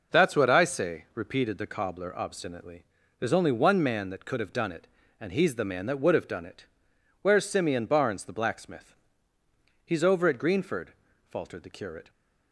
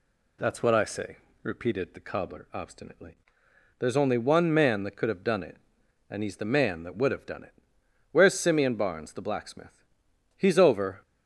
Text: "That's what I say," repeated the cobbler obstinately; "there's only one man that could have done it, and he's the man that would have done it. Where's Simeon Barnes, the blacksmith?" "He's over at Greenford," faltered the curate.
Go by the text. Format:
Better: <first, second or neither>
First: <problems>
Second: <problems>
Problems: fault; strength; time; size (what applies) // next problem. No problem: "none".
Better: first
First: none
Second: stops before "at Greenford faltered the curate"; at 11.0 s